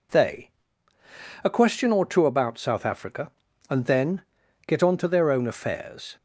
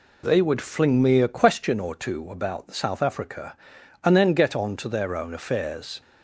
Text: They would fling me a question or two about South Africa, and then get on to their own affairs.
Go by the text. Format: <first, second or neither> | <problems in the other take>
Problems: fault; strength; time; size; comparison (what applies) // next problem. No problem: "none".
second | skips "would fling me"; at 0.9 s // pauses between "then" and "get"; at 4.2 s; 0.44 s long